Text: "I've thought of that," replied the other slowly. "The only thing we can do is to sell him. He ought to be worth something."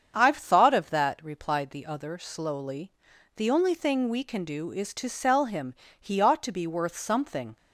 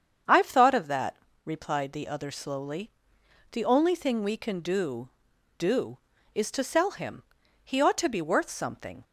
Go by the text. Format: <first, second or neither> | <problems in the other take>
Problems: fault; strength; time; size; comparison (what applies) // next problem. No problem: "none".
first | starts louder than the rest; strong; until 1.5 s; 7.5 dB; strong in the first // says "do" twice; at 5.5 s